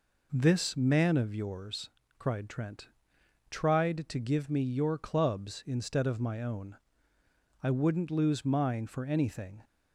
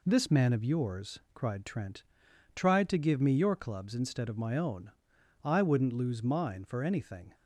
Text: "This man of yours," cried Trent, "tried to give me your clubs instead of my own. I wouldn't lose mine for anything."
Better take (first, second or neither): neither